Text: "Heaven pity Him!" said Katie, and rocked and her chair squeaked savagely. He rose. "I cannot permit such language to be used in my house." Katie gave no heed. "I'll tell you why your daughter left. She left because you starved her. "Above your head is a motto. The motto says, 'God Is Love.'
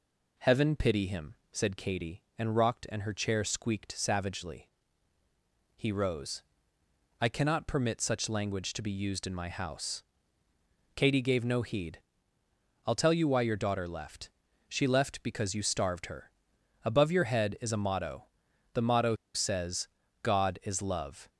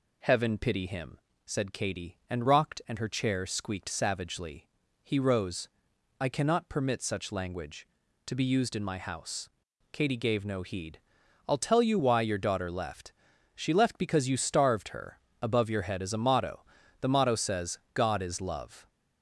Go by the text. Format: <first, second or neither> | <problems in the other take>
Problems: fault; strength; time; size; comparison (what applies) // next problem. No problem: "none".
second | pauses between "motto" and "says"; slight; at 19.1 s; 0.19 s long